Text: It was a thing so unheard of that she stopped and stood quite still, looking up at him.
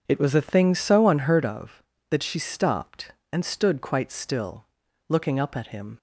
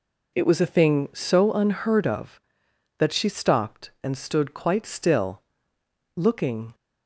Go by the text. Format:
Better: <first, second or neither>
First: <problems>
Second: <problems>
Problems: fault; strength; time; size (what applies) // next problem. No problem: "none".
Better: first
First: none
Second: stops before "up at him"; at 6.7 s